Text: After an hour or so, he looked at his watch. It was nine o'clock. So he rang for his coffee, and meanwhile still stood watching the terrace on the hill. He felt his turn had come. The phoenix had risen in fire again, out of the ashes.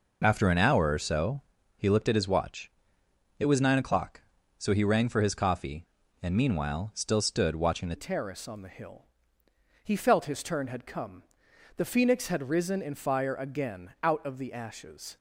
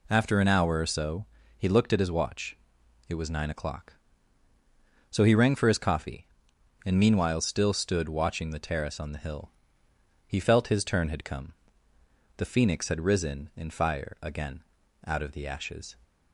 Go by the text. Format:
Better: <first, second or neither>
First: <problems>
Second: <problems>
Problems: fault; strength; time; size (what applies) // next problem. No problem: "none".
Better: second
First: changes voice at "terrace"; from 7.9 s on; 7.2 s long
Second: none